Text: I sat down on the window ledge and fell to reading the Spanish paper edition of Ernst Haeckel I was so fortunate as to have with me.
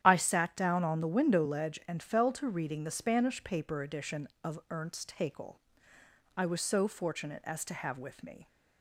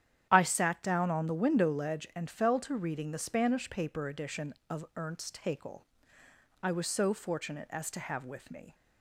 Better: neither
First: starts louder than the rest; strong; until 1.0 s; 10.5 dB // pauses between "Haeckel" and "I"; noticeable; at 5.5 s; 0.78 s long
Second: starts louder than the rest; strong; until 1.3 s; 10 dB // pauses between "Haeckel" and "I"; noticeable; at 5.8 s; 0.78 s long

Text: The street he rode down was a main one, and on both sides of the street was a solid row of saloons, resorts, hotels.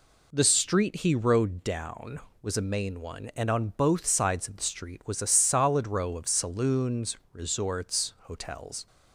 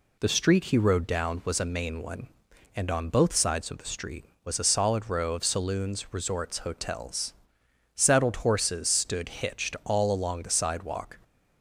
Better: first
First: none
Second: goes on to say "Saddled horses stood hitched all along the sidewalk"; strong; from 7.9 s on; 3.2 s long

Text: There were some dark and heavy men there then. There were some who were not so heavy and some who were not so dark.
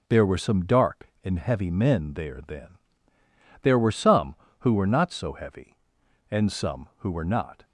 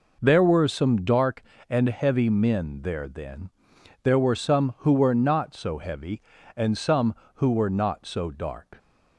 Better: second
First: stops before "so dark"; at 7.6 s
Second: none

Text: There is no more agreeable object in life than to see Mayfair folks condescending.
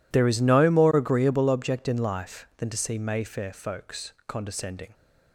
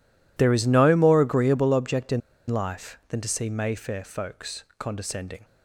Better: first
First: pauses between "folks" and "condescending"; slight; at 4.1 s; 0.16 s long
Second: pauses between "in" and "life"; slight; at 2.2 s; 0.28 s long // pauses between "folks" and "condescending"; slight; at 4.6 s; 0.16 s long

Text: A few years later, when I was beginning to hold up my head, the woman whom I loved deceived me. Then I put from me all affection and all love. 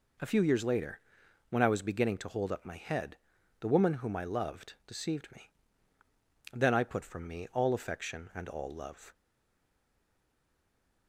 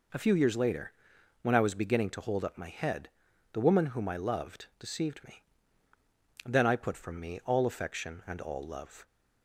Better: second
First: stays silent after the last word; noticeable; from 9.1 s on; 1.9 s long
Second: none

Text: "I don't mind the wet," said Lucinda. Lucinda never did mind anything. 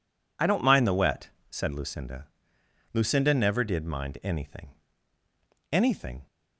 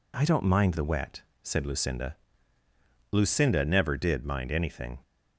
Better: second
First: says "anything" twice; at 5.7 s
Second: none

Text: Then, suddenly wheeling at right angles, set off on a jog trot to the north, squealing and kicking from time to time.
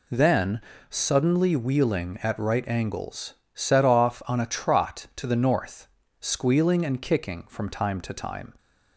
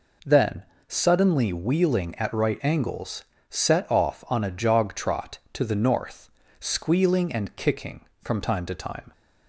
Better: second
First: skips "jog"; at 4.4 s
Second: none

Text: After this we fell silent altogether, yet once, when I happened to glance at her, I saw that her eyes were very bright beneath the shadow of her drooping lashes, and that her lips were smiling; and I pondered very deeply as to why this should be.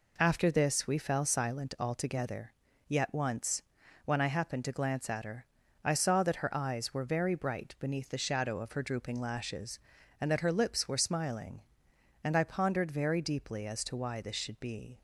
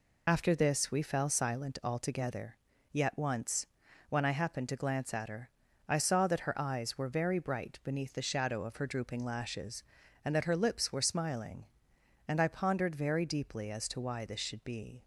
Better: first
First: none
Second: loses the start of "After"; at 0.2 s; 75 ms

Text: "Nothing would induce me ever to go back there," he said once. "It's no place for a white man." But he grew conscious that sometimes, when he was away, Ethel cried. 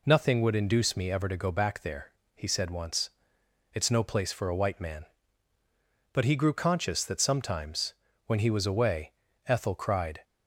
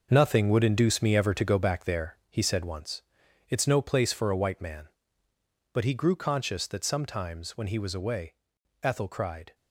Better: first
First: none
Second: gets quieter; strong; throughout; 10 dB

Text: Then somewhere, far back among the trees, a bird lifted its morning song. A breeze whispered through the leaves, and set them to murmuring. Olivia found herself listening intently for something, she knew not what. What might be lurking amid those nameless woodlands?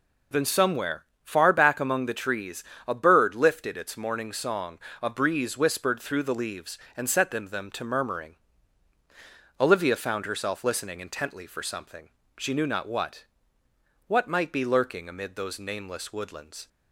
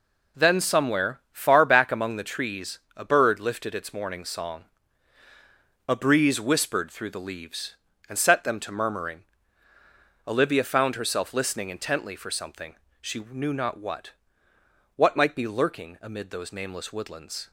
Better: second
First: says "them" twice; at 7.4 s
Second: none

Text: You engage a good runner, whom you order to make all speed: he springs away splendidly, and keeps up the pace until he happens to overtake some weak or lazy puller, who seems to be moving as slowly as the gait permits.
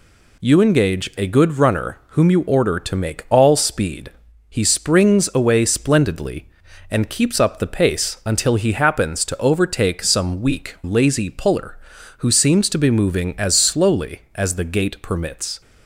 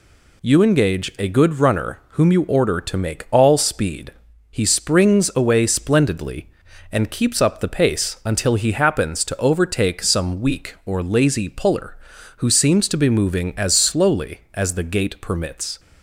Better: second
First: skips "or"; at 10.7 s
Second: none

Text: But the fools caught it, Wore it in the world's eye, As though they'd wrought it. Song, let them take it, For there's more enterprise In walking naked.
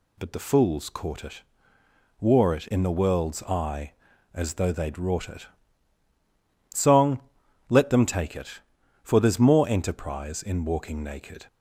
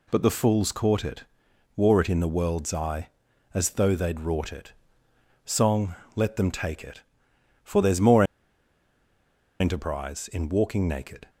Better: first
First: none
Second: pauses between "more" and "enterprise"; strong; at 8.2 s; 1.3 s long

